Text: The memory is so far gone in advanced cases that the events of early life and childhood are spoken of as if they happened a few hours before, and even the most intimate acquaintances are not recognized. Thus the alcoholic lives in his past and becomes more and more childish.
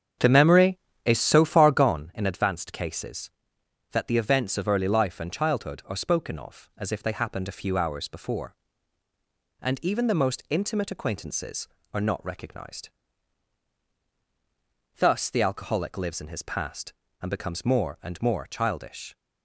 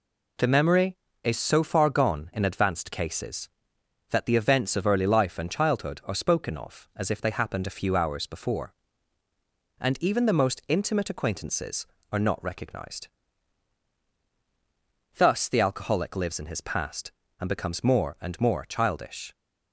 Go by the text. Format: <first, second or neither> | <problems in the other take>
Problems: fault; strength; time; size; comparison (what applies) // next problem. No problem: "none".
second | starts louder than the rest; strong; until 2.0 s; 8 dB